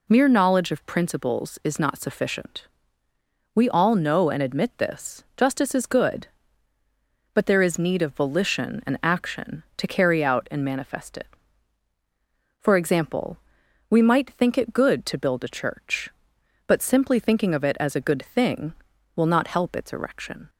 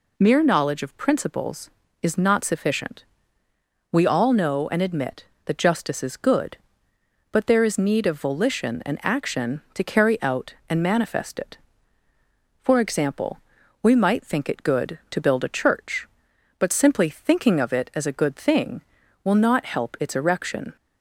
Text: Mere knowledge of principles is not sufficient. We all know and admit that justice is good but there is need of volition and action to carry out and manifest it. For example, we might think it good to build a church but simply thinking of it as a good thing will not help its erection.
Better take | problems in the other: second | says "this" for "that"; at 4.7 s

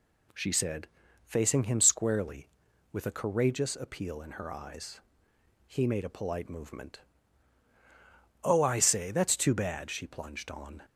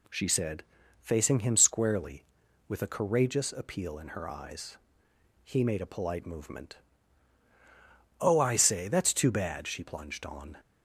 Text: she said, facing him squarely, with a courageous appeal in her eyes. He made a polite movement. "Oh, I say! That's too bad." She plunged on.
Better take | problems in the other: neither | none

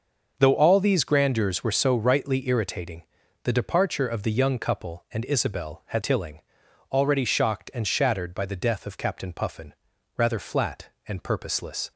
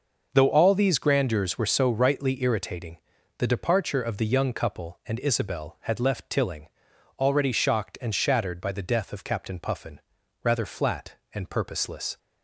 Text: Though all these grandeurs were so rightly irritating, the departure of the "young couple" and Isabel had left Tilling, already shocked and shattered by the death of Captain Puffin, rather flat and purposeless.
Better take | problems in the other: second | starts louder than the rest; noticeable; until 1.3 s; 6 dB // skips "left"; at 6.0 s

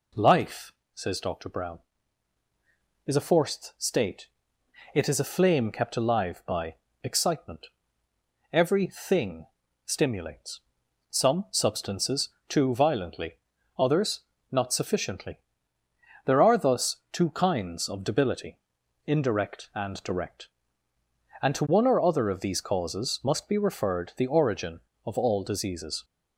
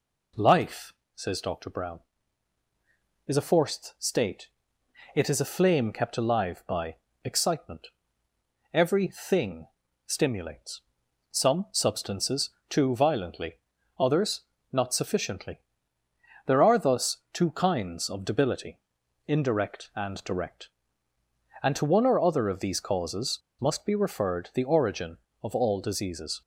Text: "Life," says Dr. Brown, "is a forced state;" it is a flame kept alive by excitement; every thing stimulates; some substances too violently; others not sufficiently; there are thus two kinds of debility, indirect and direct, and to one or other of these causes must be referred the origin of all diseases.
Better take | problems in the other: first | pauses between "by" and "excitement"; slight; at 6.9 s; 0.28 s long; slight in the first // pauses between "thing" and "stimulates"; at 9.6 s; 0.40 s long; also in the first // pauses between "substances" and "too"; slight; at 12.4 s; 0.18 s long; slight in the first // pauses between "others" and "not"; slight; at 14.4 s; 0.30 s long; slight in the first // pauses between "causes" and "must"; slight; at 23.3 s; 0.24 s long

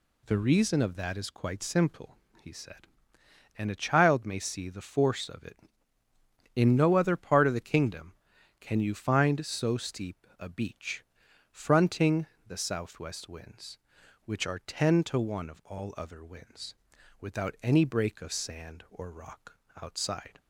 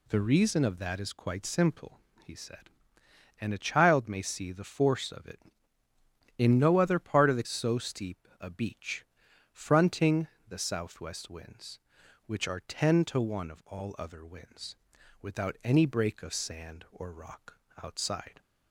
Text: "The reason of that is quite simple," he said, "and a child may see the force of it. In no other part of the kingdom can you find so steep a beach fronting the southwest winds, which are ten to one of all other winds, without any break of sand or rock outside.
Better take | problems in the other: first | skips "kingdom can you find"; at 7.4 s // pauses between "beach" and "fronting"; noticeable; at 9.0 s; 0.48 s long; noticeable in the first // pauses between "fronting" and "the"; slight; at 10.2 s; 0.22 s long; slight in the first // pauses between "rock" and "outside"; slight; at 17.5 s; 0.24 s long; slight in the first

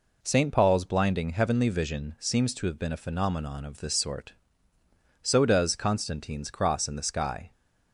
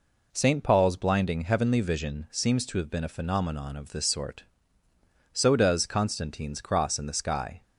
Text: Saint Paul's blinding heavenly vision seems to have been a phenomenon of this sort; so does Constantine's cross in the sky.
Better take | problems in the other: neither | none

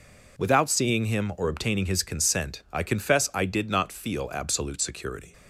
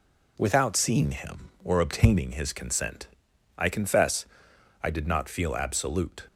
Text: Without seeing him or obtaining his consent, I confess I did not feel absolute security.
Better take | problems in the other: first | pauses between "confess" and "I"; noticeable; at 4.2 s; 0.58 s long // stops before "security"; at 6.2 s

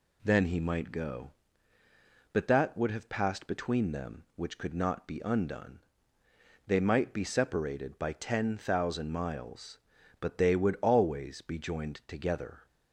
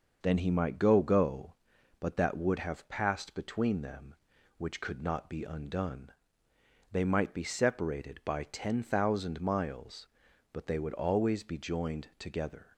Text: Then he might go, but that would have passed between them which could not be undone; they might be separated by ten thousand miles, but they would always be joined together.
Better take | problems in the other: first | says "go" twice; at 1.0 s

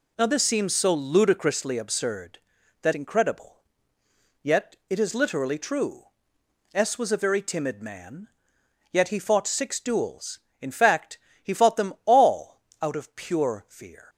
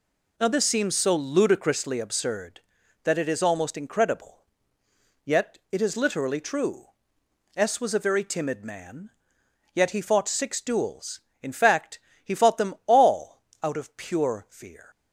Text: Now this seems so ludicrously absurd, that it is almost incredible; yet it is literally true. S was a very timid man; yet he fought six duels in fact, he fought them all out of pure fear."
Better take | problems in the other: second | skips "it is almost"; at 2.9 s // pauses between "yet" and "it"; slight; at 4.7 s; 0.16 s long; slight in the second // pauses between "all" and "out"; slight; at 12.6 s; 0.20 s long; slight in the second

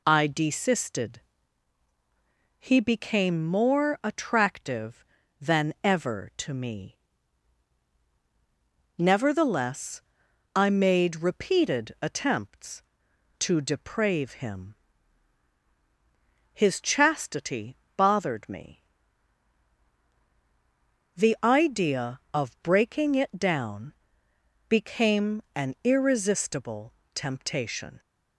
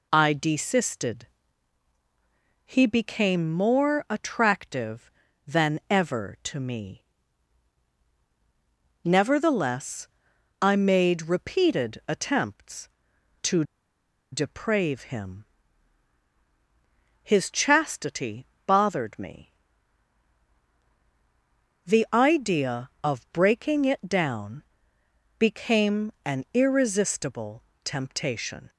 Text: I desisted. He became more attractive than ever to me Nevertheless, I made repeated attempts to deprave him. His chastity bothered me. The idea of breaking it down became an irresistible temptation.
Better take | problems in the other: first | pauses between "me" and "Nevertheless"; strong; at 7.0 s; 2.0 s long; strong in the first // pauses between "to" and "deprave"; noticeable; at 13.6 s; 0.69 s long // pauses between "chastity" and "bothered"; slight; at 18.4 s; 0.22 s long; slight in the first // pauses between "down" and "became"; noticeable; at 24.6 s; 0.78 s long; noticeable in the first // pauses between "irresistible" and "temptation"; slight; at 27.6 s; 0.20 s long; slight in the first

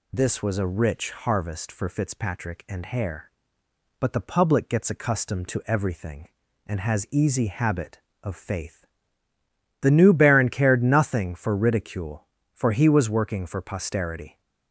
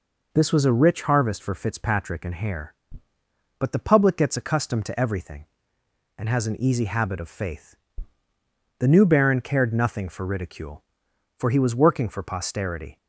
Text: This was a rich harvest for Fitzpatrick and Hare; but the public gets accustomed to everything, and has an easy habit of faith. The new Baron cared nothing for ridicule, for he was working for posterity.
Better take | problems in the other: second | skips "an"; at 7.0 s

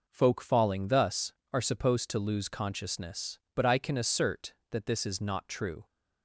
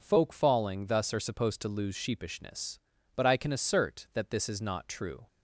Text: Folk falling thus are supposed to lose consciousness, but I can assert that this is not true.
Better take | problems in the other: first | says "sheepishness" for "consciousness"; at 1.9 s

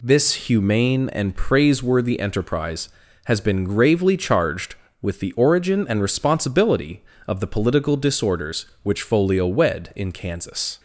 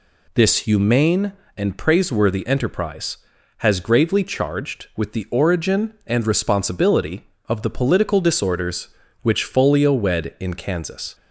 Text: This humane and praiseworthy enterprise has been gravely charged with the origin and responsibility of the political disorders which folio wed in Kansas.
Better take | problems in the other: first | skips "been"; at 3.8 s

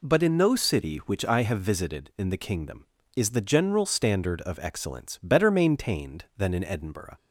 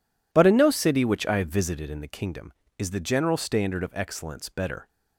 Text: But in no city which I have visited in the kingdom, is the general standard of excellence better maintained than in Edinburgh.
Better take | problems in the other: first | stops before "maintained than in Edinburgh"; at 4.8 s

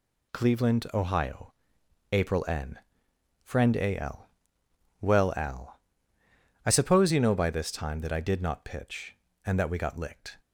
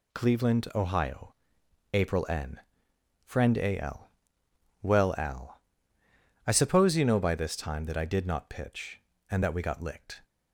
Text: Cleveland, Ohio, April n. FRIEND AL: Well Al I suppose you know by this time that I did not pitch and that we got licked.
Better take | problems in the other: neither | pauses between "Al" and "I"; noticeable; the same in both

